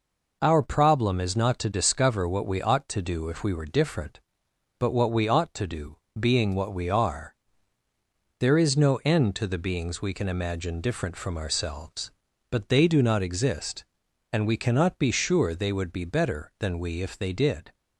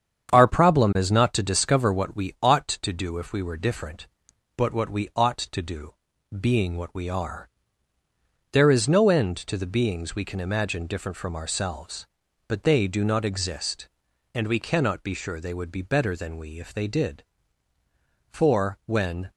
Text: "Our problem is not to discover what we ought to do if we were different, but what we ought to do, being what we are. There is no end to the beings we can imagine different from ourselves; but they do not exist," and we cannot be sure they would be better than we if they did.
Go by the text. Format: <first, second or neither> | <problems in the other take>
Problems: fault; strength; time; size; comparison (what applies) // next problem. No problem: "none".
first | starts louder than the rest; strong; until 1.3 s; 8 dB // goes on to say "For when"; noticeable; from 18.3 s on; 1.0 s long